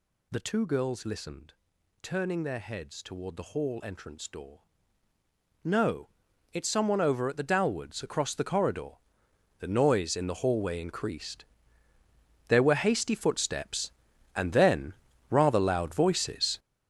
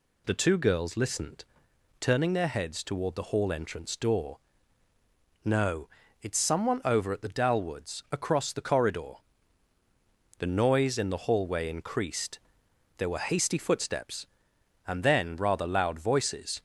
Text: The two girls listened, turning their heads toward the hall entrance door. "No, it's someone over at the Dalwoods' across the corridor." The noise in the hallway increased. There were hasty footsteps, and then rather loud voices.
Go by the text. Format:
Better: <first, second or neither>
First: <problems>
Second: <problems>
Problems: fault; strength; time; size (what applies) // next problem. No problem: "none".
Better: second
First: gets louder; strong; throughout; 10.5 dB // pauses between "then" and "rather"; at 14.9 s; 0.38 s long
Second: none